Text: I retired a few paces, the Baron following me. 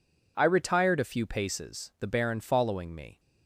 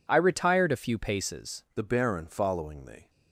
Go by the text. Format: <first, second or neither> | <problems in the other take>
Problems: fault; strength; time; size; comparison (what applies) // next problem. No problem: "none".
first | changes voice at "the"; from 1.7 s on; 1.3 s long